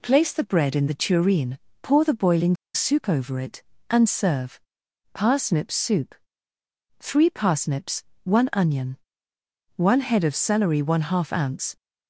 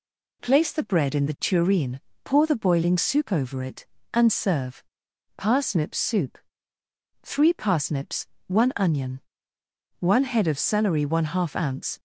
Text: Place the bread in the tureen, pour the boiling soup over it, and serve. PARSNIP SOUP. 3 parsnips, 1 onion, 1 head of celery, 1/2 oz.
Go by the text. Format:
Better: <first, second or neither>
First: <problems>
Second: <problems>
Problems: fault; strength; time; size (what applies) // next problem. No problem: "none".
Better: second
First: pauses between "boiling" and "soup"; slight; at 2.5 s; 0.19 s long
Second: none